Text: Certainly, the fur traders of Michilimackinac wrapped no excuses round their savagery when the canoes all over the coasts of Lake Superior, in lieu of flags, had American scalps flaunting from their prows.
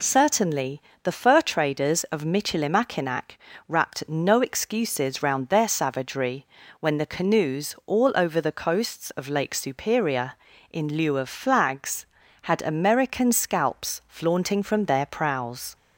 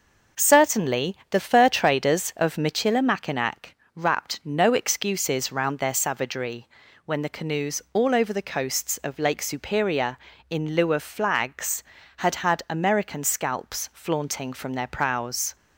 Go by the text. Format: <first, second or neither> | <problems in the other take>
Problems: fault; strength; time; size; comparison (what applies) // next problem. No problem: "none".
first | pauses between "Michilimackinac" and "wrapped"; slight; at 3.7 s; 0.22 s long; slight in the first // pauses between "savagery" and "when"; at 6.6 s; 0.38 s long; slight in the first // says "had" twice; at 12.4 s